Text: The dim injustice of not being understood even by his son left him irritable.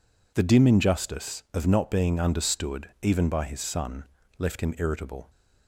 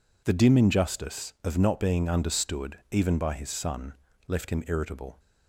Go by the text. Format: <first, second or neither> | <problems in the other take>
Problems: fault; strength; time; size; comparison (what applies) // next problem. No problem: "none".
neither | pauses between "son" and "left"; slight; the same in both